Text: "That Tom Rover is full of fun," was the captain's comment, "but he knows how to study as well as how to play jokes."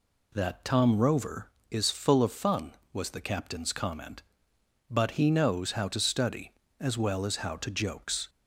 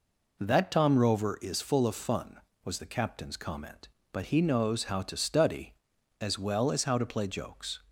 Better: second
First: skips "play"; at 7.6 s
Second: none

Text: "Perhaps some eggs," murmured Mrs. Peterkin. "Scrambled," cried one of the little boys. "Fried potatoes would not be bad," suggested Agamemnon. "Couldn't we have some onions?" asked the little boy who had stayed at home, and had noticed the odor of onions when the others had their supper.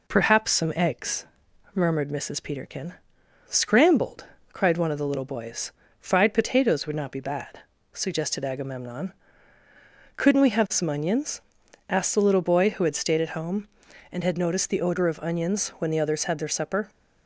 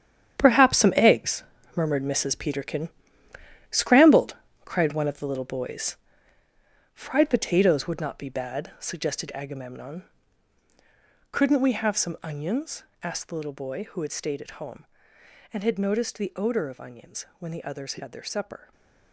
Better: first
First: none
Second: gets quieter; strong; throughout; 11.5 dB

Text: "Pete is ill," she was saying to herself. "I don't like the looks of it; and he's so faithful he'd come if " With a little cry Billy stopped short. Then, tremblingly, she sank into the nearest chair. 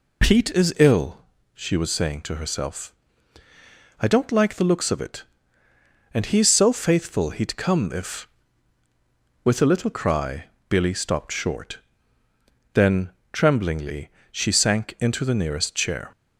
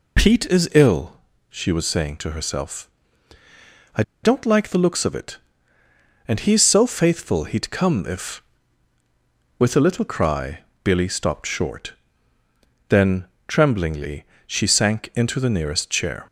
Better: first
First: pauses between "cry" and "Billy"; slight; at 10.4 s; 0.24 s long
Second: pauses between "I" and "don't"; slight; at 4.0 s; 0.21 s long // pauses between "cry" and "Billy"; slight; at 10.5 s; 0.24 s long

